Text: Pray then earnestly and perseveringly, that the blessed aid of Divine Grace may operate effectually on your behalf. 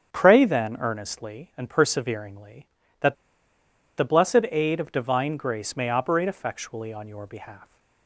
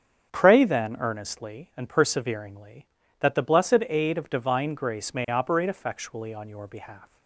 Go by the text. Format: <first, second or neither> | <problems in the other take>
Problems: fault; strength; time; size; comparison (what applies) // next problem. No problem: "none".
second | starts louder than the rest; strong; until 1.1 s; 7 dB; strong in the second // pauses between "that" and "the"; noticeable; at 3.1 s; 0.81 s long